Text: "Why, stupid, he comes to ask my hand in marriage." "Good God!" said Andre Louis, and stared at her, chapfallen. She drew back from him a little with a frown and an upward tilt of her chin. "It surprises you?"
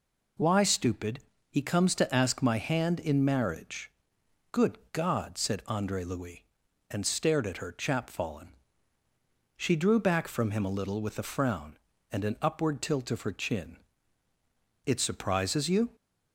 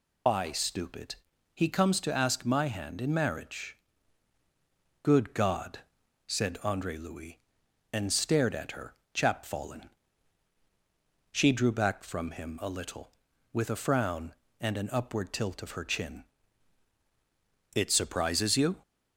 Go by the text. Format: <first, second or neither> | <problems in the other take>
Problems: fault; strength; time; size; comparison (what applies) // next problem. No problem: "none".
first | loses the start of "Why"; at 0.2 s; 120 ms